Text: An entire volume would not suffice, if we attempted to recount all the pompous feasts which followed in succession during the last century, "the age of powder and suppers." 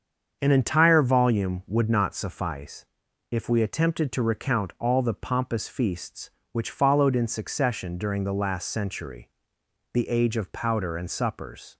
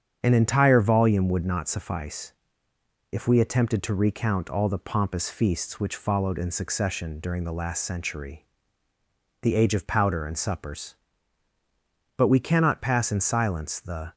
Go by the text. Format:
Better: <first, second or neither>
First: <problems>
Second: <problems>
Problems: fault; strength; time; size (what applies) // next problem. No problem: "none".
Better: first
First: starts louder than the rest; until 1.4 s; 7 dB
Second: starts louder than the rest; strong; until 1.2 s; 8 dB // goes on to say "But we cannot pass in silence the"; strong; from 12.1 s on; 1.9 s long